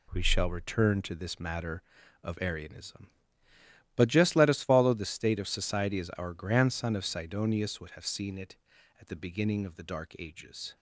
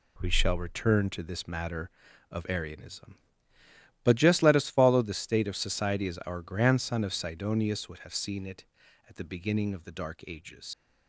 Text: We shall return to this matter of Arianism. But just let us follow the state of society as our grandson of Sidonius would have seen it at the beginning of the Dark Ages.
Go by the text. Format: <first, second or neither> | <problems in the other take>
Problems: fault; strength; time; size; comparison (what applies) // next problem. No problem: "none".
first | leaves "Ages" unfinished; at 10.7 s; 105 ms